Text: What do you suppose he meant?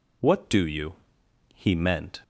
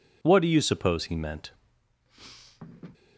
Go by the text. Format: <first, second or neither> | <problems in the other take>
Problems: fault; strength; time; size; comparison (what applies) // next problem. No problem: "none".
second | skips "suppose"; at 1.2 s